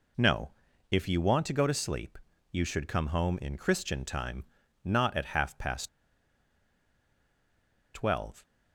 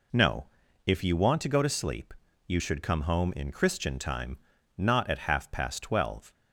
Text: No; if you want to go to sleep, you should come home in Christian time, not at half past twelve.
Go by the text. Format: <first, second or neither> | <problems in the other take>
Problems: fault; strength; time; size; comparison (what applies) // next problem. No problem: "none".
second | pauses between "past" and "twelve"; strong; at 5.8 s; 2.0 s long